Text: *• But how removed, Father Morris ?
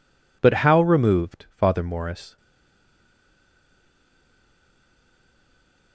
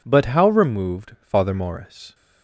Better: second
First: stays silent after the last word; strong; from 2.3 s on; 3.6 s long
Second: none

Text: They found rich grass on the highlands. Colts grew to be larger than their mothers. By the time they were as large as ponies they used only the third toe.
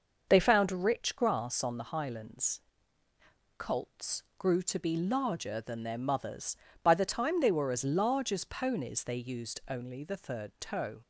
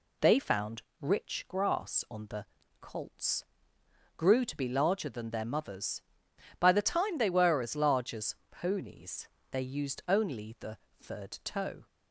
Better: first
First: none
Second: pauses between "found" and "rich"; slight; at 0.8 s; 0.18 s long // skips "highlands"; at 2.6 s // pauses between "Colts" and "grew"; noticeable; at 3.4 s; 0.74 s long // pauses between "as" and "ponies"; slight; at 8.3 s; 0.16 s long // pauses between "ponies" and "they"; slight; at 9.2 s; 0.24 s long // pauses between "the" and "third"; slight; at 10.7 s; 0.22 s long

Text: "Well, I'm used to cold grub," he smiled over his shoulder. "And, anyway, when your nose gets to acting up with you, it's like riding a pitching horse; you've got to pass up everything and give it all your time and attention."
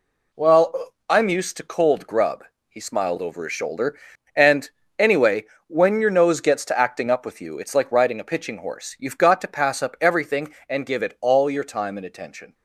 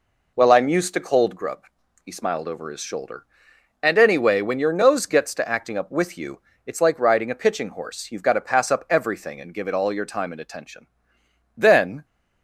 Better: first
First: none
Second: goes on to say "Then"; from 11.5 s on; 0.50 s long

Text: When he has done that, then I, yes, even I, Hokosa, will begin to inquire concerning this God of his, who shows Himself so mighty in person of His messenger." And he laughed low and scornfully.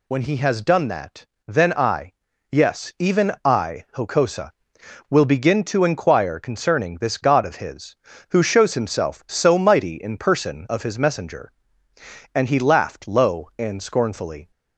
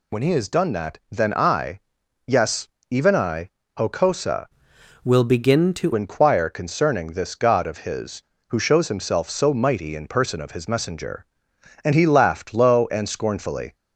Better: first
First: none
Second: changes voice from "will" to "to"; from 5.0 to 5.9 s; 0.9 s long

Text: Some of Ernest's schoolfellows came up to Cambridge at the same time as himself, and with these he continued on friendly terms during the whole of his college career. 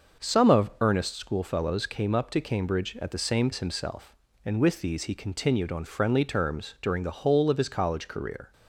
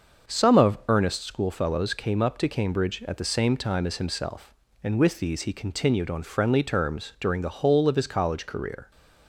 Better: second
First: starts louder than the rest; until 1.3 s; 6 dB // skips "time"; at 3.5 s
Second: starts louder than the rest; until 1.3 s; 6 dB

